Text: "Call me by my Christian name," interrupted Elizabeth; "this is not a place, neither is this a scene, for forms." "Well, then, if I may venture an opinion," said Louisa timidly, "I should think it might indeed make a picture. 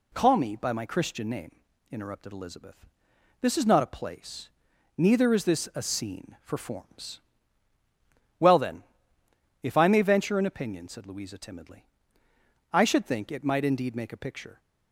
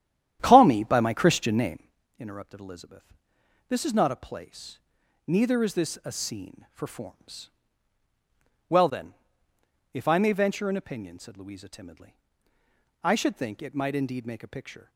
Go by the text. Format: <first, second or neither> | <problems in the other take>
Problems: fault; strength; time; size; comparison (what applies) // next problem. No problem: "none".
first | starts louder than the rest; strong; until 2.0 s; 11 dB